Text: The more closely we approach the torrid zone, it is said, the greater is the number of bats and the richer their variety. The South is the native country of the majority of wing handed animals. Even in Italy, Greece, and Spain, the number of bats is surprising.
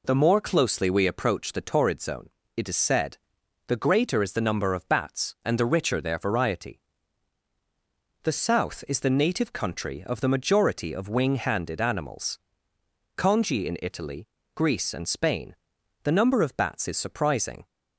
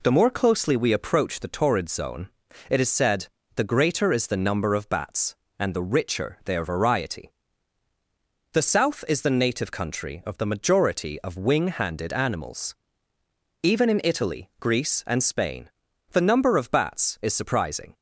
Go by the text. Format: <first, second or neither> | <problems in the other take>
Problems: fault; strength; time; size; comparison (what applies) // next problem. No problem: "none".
second | says "Congi" for "Even"; at 13.1 s